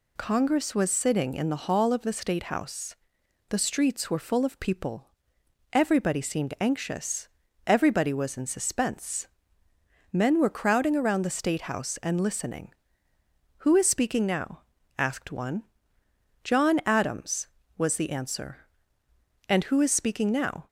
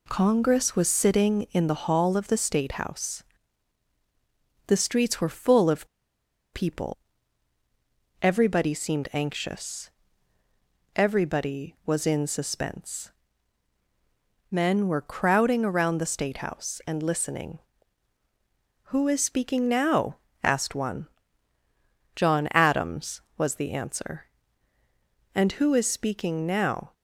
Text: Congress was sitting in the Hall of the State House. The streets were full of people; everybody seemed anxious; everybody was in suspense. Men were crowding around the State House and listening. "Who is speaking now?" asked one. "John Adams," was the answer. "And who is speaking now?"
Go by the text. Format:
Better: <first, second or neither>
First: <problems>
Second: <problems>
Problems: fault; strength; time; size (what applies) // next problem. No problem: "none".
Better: first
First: none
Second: pauses between "of" and "people"; noticeable; at 5.8 s; 0.67 s long